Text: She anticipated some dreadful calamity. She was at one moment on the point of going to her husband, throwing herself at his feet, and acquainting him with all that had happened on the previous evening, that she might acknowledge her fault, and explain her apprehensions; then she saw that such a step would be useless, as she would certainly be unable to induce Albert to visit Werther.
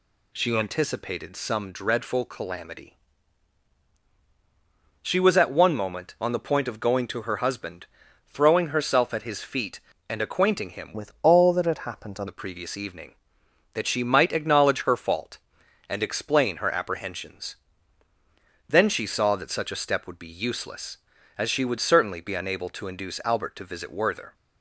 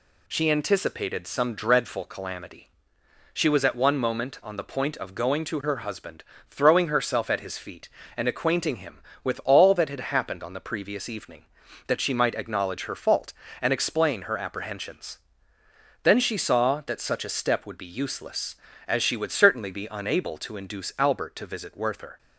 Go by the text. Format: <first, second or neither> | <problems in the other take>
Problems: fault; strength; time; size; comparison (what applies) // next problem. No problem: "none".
second | changes voice from "with" to "on"; from 10.9 to 12.2 s; 1.3 s long